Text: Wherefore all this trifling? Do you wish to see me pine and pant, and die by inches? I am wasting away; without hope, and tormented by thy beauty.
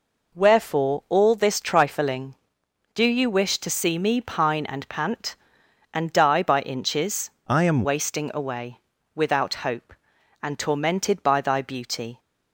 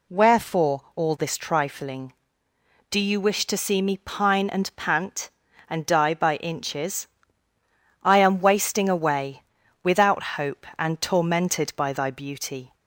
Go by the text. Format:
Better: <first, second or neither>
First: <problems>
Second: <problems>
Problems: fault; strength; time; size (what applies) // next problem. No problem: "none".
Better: second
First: changes voice from "I" to "am"; from 7.4 to 7.8 s; 0.4 s long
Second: none